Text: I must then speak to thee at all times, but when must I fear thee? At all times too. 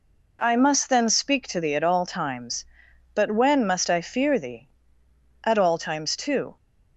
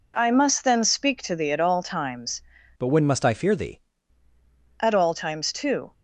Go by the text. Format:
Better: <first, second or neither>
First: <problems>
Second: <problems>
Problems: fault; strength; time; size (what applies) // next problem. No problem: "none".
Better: first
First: none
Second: changes voice from "but" to "thee"; from 2.7 to 3.7 s; 1.0 s long